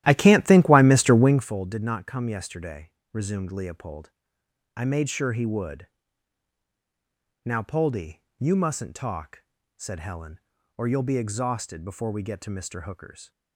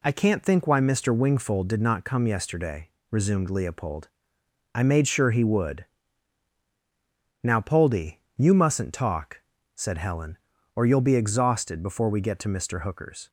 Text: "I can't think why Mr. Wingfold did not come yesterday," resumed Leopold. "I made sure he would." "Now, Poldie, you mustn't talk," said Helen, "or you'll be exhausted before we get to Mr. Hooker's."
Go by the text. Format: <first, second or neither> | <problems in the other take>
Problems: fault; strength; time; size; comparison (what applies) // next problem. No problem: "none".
second | starts louder than the rest; strong; until 1.5 s; 13.5 dB